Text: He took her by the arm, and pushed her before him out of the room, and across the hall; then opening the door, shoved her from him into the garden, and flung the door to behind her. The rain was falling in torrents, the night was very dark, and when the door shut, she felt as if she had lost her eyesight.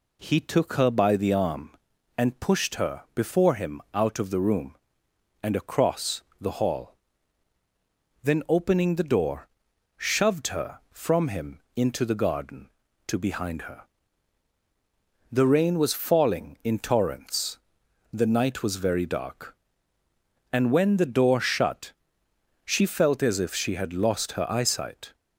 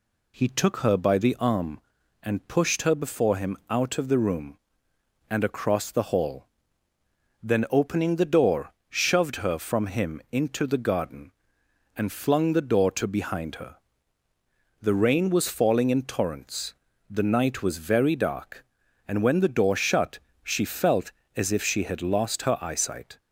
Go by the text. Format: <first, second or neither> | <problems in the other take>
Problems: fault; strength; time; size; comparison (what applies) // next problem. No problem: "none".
second | pauses between "across" and "the"; slight; at 6.2 s; 0.18 s long // skips "and flung the door"; at 12.8 s